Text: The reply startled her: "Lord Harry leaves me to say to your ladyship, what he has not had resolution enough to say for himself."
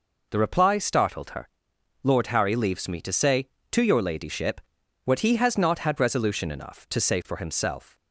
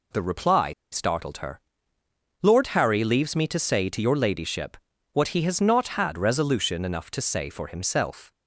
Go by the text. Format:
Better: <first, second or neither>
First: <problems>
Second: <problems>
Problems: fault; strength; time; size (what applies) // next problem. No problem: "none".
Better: first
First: none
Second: pauses between "reply" and "startled"; slight; at 0.7 s; 0.19 s long